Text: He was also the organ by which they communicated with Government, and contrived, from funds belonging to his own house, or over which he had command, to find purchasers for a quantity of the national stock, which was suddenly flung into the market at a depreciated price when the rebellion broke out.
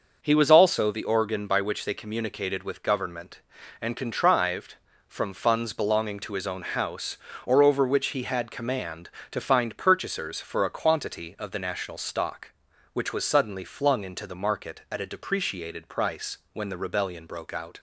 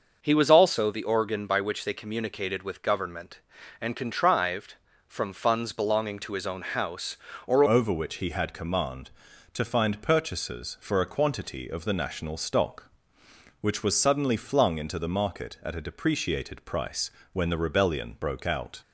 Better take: first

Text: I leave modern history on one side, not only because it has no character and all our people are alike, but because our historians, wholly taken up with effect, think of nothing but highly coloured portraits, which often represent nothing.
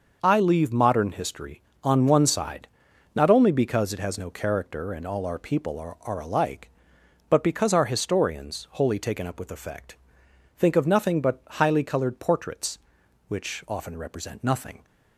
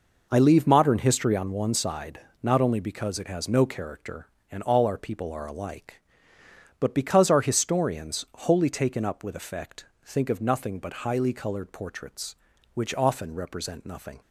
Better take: second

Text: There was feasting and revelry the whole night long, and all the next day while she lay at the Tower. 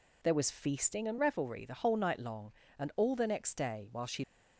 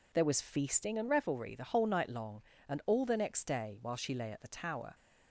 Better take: second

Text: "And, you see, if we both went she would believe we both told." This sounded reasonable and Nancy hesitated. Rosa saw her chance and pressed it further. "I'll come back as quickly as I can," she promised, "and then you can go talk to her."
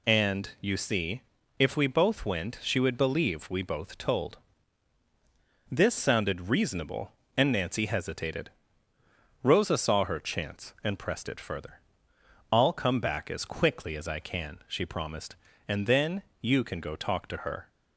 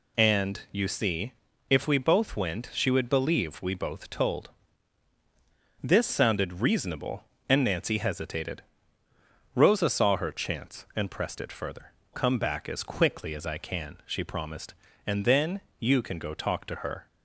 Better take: first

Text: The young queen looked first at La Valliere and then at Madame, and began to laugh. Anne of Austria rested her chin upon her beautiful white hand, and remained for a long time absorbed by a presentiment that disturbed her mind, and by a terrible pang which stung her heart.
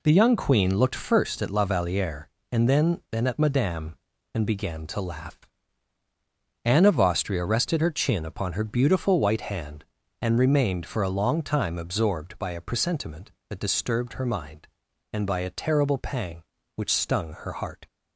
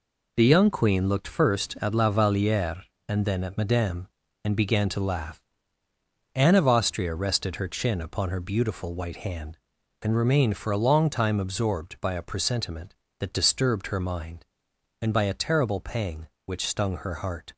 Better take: second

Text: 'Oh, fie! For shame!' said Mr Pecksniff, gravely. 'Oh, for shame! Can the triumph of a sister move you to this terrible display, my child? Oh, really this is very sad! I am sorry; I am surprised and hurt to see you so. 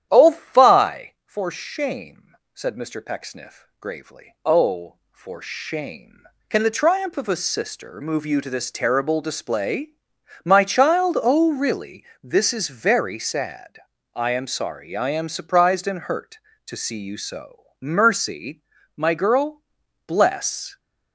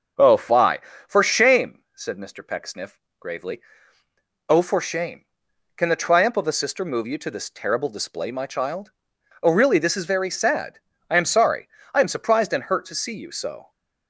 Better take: second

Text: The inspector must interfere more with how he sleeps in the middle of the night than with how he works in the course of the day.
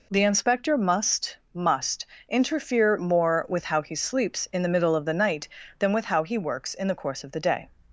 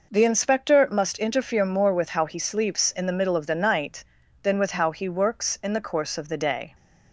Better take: second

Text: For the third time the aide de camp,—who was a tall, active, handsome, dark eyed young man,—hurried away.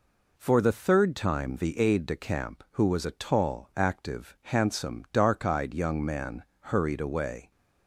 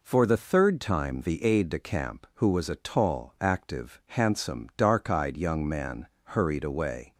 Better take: neither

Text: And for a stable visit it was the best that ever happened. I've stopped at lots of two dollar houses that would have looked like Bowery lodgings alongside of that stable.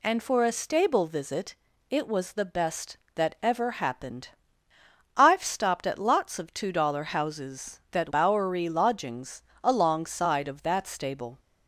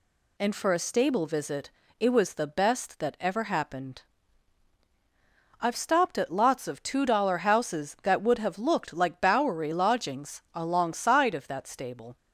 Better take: second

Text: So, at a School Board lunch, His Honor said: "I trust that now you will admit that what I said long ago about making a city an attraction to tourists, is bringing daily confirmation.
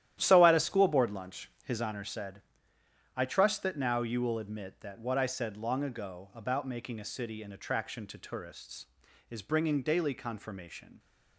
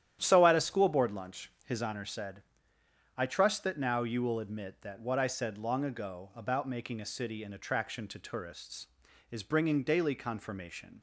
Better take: second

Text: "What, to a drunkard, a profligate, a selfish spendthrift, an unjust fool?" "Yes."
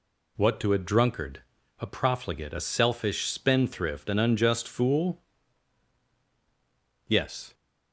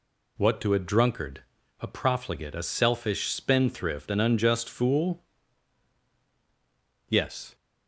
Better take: neither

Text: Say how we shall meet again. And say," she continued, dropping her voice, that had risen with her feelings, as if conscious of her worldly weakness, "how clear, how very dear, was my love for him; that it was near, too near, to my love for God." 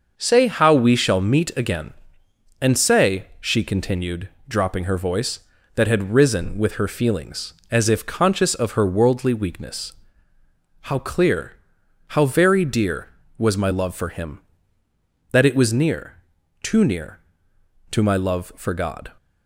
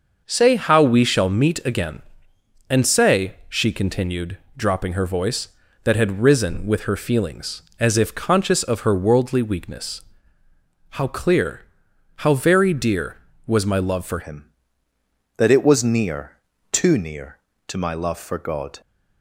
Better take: first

